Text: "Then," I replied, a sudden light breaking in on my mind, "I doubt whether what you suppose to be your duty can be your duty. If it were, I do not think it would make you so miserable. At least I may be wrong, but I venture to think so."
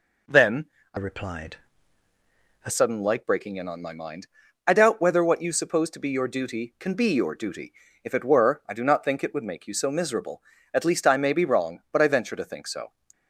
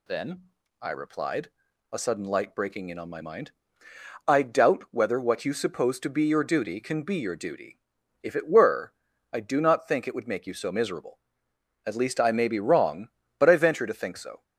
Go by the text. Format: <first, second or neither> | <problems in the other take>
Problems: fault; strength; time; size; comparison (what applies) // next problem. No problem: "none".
second | changes voice from "replied" to "a"; from 0.9 to 2.7 s; 1.8 s long